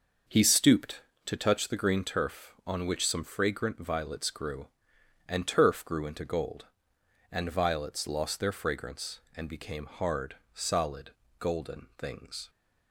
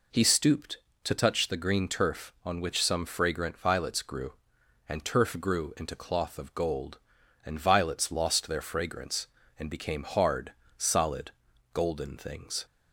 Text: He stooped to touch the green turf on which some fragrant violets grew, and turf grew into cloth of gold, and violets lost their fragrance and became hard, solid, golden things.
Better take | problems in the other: second | skips "cloth of"; at 6.2 s

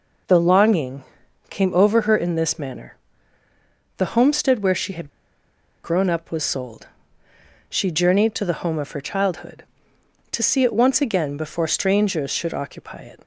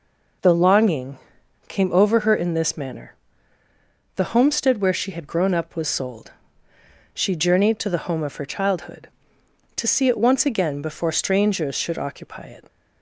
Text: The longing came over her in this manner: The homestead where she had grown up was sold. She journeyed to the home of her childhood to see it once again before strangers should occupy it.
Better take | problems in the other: second | pauses between "longing" and "came"; noticeable; at 1.0 s; 0.46 s long; noticeable in the second // pauses between "had" and "grown"; noticeable; at 5.0 s; 0.76 s long

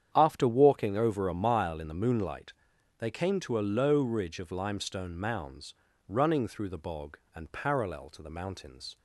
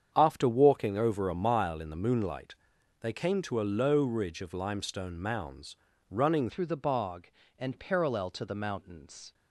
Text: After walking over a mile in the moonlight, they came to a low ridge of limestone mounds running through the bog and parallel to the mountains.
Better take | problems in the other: first | starts louder than the rest; strong; until 1.1 s; 8 dB; strong in the first // pauses between "mounds" and "running"; slight; at 5.7 s; 0.36 s long; slight in the first // changes voice at "through"; from 6.4 s on; 2.9 s long

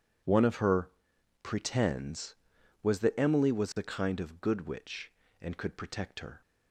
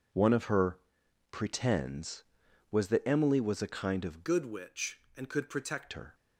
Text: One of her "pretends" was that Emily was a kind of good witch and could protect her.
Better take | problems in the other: first | pauses between "her" and "pretends"; noticeable; at 0.7 s; 0.52 s long; noticeable in the first // changes voice from "good" to "protect"; from 4.2 to 5.9 s; 1.7 s long

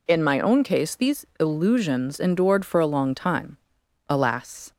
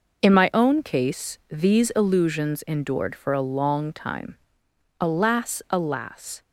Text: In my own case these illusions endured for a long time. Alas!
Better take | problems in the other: first | says "Alas" twice; at 5.6 s

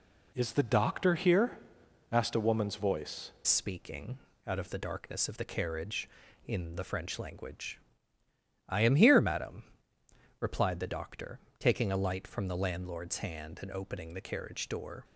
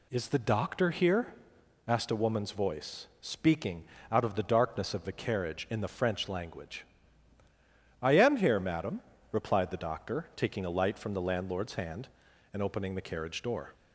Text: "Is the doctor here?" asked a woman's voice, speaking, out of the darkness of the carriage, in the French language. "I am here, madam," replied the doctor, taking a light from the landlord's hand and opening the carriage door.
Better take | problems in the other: second | changes voice at "speaking"; from 3.4 s on; 11.6 s long

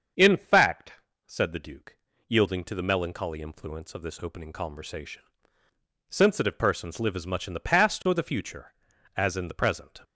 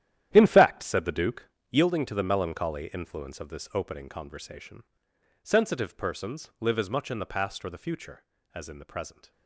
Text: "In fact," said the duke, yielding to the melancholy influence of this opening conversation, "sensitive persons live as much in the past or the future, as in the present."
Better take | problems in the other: first | gets quieter; strong; throughout; 13 dB // starts louder than the rest; strong; until 1.3 s; 11.5 dB; also in the first

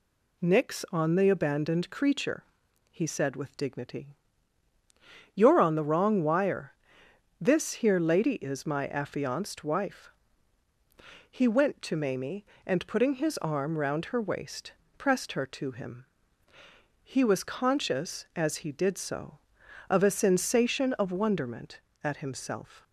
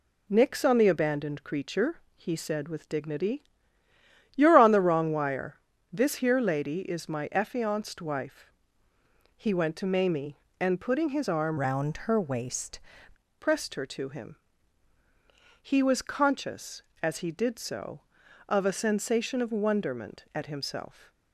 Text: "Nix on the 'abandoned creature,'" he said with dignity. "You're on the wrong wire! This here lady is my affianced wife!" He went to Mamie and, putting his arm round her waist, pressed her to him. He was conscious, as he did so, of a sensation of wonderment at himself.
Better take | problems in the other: first | changes voice from "round" to "waist"; from 11.5 to 12.7 s; 1.2 s long

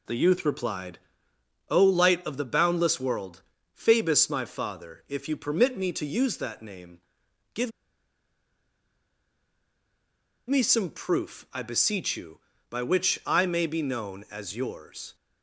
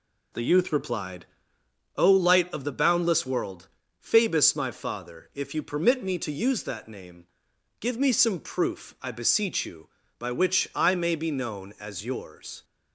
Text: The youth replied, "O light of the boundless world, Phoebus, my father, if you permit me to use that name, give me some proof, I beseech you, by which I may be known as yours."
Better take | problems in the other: second | pauses between "give" and "me"; strong; at 7.7 s; 2.7 s long

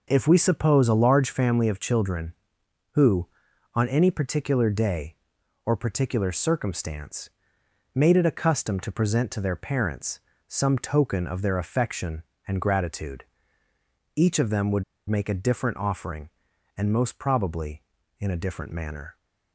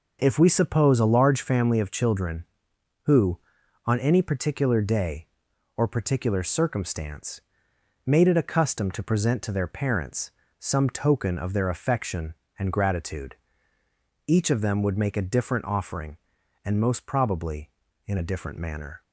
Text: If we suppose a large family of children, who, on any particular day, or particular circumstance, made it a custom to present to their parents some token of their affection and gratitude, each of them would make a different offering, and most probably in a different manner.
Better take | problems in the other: second | pauses between "parents" and "some"; slight; at 10.1 s; 0.28 s long; slight in the second // pauses between "would" and "make"; slight; at 14.8 s; 0.26 s long

